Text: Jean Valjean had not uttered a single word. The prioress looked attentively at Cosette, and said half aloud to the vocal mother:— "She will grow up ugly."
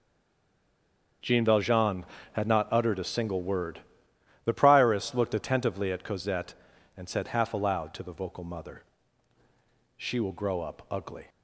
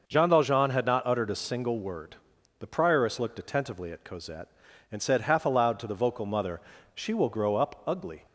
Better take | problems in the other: second | stays silent before the first word; noticeable; until 1.2 s; 1.2 s long // starts louder than the rest; until 2.5 s; 6.5 dB

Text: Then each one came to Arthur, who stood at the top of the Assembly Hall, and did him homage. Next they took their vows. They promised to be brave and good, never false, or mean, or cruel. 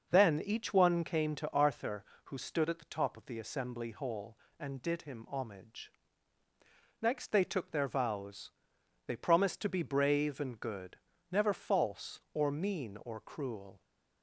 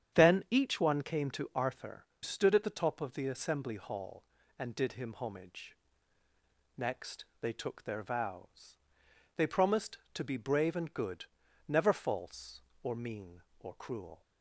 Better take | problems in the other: first | starts louder than the rest; strong; until 1.2 s; 8.5 dB // skips "who"; at 2.1 s // pauses between "Next" and "they"; slight; at 7.2 s; 0.16 s long

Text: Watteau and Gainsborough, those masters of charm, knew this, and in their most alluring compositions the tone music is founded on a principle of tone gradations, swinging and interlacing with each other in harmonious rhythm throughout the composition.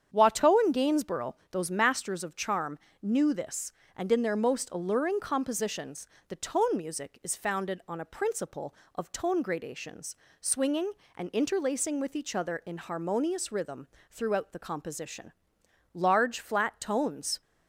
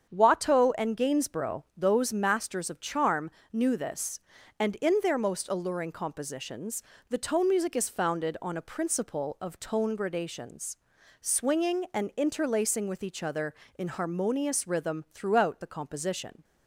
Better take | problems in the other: second | starts louder than the rest; strong; until 1.1 s; 8 dB; strong in the second // pauses between "compositions" and "the"; slight; at 6.0 s; 0.22 s long; slight in the second // pauses between "rhythm" and "throughout"; slight; at 13.8 s; 0.22 s long // goes on to say "Large flat tones"; from 15.9 s on; 1.4 s long

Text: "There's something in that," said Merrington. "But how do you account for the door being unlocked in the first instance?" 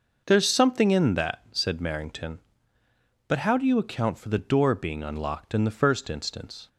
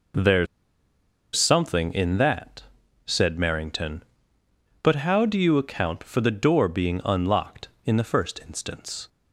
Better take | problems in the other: first | pauses between "There's" and "something"; noticeable; at 0.4 s; 0.89 s long

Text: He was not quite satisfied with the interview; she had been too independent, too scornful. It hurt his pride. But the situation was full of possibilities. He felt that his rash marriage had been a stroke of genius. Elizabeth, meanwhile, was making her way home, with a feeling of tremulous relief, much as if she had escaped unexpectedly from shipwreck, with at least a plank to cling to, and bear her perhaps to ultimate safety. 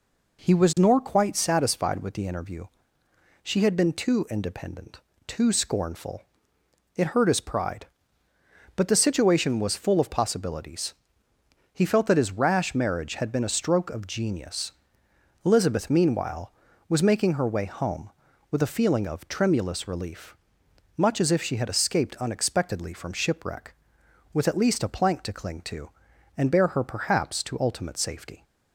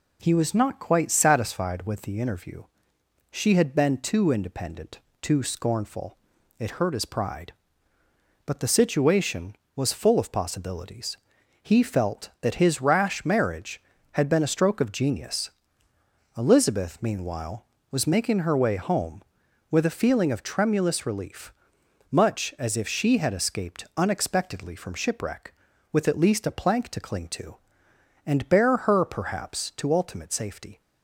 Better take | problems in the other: second | says "nor" for "not"; at 0.7 s

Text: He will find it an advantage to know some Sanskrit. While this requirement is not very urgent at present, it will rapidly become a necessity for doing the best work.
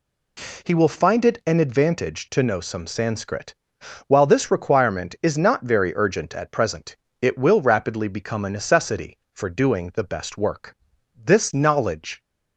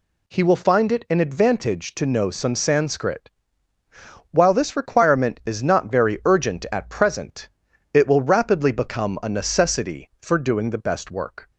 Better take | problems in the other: second | goes on to say "This knowledge"; noticeable; from 11.1 s on; 1.0 s long

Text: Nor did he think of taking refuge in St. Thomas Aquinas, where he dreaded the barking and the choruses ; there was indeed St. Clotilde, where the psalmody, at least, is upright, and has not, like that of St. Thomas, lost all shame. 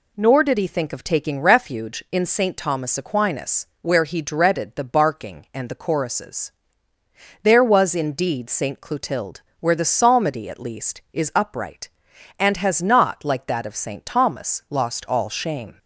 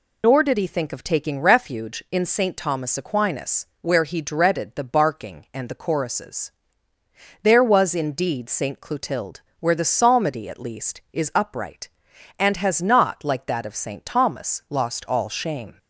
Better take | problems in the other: first | loses the start of "Nor"; at 0.2 s; 85 ms

